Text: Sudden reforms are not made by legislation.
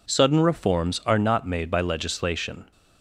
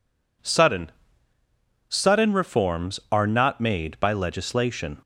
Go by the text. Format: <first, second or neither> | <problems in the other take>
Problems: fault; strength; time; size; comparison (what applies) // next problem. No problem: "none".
first | says "Sudden" twice; at 1.8 s